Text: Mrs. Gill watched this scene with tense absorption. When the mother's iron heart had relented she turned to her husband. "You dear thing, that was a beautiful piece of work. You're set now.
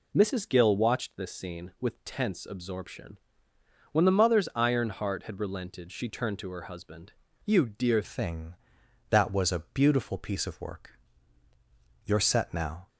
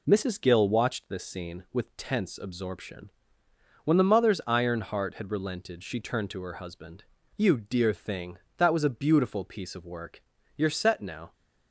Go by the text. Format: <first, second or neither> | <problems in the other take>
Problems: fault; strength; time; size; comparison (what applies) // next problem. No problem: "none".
second | changes voice at "thing"; from 8.0 s on; 4.8 s long